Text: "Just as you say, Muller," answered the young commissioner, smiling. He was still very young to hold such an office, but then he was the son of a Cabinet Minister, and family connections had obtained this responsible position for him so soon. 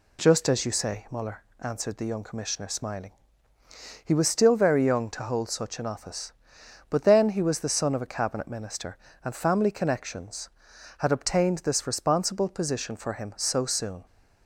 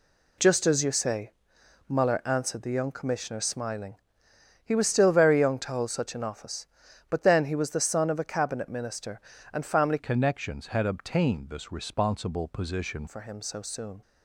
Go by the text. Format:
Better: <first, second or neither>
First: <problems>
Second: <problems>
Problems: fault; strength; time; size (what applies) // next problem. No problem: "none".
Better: first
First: none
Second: changes voice from "connections" to "position"; from 9.9 to 13.0 s; 3.1 s long